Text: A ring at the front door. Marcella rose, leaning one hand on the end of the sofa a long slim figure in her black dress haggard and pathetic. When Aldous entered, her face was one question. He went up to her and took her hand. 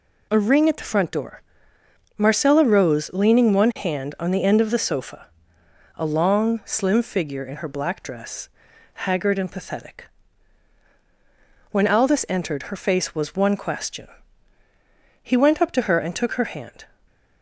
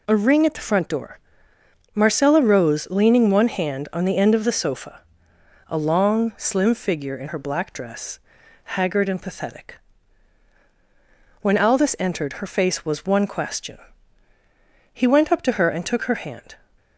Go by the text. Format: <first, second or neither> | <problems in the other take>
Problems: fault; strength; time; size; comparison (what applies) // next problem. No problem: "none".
neither | pauses between "sofa" and "a"; noticeable; the same in both // pauses between "dress" and "haggard"; noticeable; the same in both